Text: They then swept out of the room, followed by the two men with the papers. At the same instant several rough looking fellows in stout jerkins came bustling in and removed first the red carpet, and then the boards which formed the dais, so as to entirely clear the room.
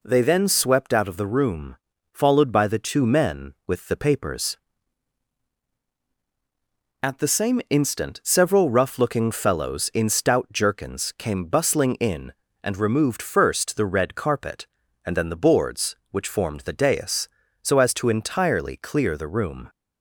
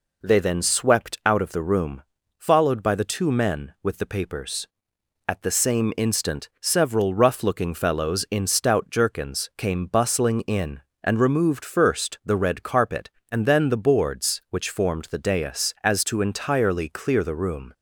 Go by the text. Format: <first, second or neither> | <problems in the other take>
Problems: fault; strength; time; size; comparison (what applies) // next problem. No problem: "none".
first | skips "so"; at 15.7 s